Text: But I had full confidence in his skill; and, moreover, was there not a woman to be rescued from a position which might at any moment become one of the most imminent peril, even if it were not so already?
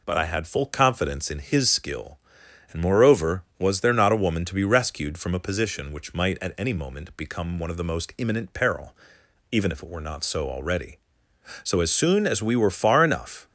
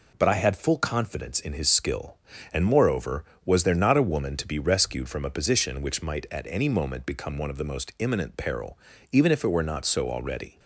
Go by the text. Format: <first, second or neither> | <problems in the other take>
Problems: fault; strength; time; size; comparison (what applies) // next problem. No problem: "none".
second | goes on to say "So as soon as we were far enough"; strong; from 11.6 s on; 1.8 s long